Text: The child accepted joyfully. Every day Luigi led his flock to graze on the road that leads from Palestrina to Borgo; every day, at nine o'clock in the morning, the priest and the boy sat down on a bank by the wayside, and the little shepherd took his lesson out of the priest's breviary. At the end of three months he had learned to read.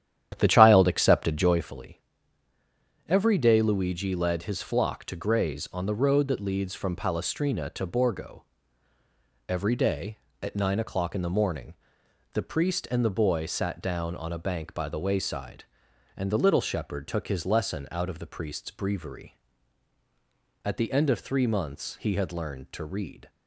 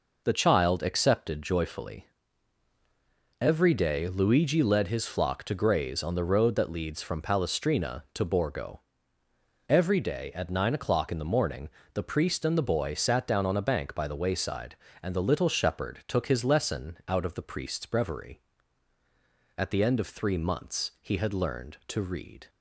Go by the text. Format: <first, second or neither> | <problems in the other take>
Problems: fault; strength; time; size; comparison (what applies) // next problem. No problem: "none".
second | starts louder than the rest; strong; until 1.7 s; 10.5 dB